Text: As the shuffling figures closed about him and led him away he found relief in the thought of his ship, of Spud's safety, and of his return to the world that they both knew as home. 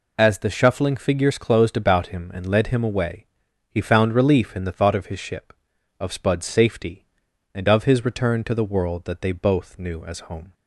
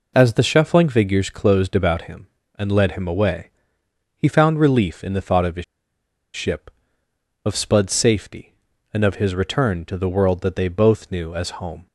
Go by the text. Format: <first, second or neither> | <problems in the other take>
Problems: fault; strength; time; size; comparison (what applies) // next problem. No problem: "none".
first | pauses between "away" and "he"; noticeable; at 3.4 s; 0.66 s long; also in the first // pauses between "his" and "ship"; noticeable; at 5.6 s; 0.70 s long